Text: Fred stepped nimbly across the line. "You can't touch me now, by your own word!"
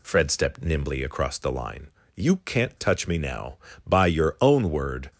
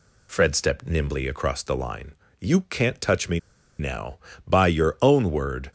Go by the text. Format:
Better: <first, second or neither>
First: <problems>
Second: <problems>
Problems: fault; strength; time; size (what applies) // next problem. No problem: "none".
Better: first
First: none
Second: pauses between "me" and "now"; at 3.3 s; 0.39 s long